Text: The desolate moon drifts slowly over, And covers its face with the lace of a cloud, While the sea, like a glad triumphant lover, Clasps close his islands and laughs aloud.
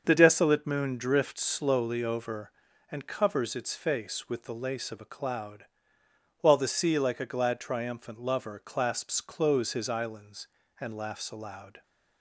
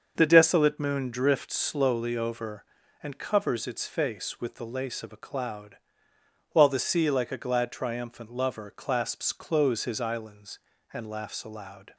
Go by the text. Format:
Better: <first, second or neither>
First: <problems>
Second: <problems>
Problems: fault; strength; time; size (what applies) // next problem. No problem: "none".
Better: neither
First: starts louder than the rest; until 1.0 s; 6.5 dB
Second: starts louder than the rest; until 1.1 s; 6.5 dB